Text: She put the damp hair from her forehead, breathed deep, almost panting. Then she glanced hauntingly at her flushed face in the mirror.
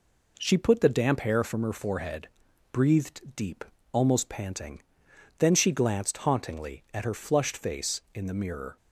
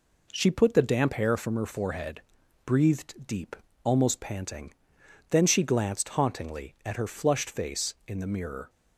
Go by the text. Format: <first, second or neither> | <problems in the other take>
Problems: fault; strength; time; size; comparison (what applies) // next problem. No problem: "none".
neither | none